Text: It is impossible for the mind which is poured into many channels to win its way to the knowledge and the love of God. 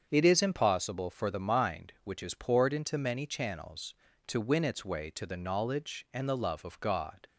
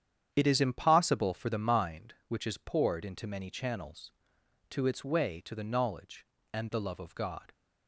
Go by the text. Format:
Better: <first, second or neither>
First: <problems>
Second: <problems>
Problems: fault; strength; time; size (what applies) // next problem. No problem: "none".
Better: first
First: starts louder than the rest; strong; until 1.1 s; 7 dB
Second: starts louder than the rest; strong; until 1.3 s; 9 dB // skips "win"; at 4.8 s